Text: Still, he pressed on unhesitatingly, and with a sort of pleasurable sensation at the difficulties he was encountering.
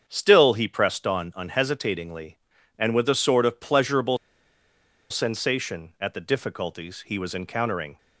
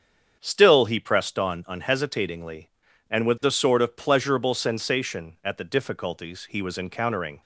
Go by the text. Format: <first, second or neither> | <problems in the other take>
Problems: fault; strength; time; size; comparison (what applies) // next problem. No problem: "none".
second | starts louder than the rest; strong; until 1.0 s; 7.5 dB; strong in the second // pauses between "pleasurable" and "sensation"; noticeable; at 4.1 s; 0.93 s long